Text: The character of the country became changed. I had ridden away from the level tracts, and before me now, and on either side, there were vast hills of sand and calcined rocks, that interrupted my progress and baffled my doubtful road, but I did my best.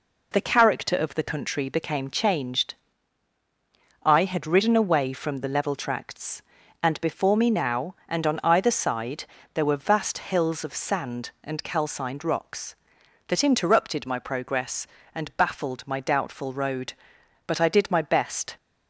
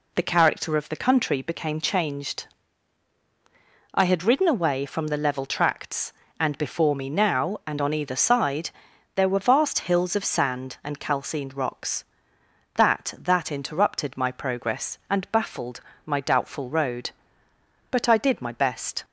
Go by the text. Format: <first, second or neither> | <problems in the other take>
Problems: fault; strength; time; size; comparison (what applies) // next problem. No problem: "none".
first | says "that" twice; at 13.1 s // pauses between "baffled" and "my"; slight; at 15.8 s; 0.26 s long